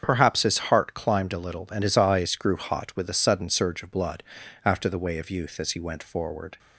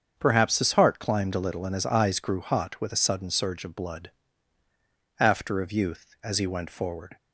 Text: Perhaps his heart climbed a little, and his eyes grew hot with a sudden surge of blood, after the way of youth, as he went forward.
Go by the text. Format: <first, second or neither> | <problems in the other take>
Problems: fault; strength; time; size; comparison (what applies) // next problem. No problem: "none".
first | starts louder than the rest; until 1.1 s; 7 dB; strong in the first // skips "the way"; at 5.6 s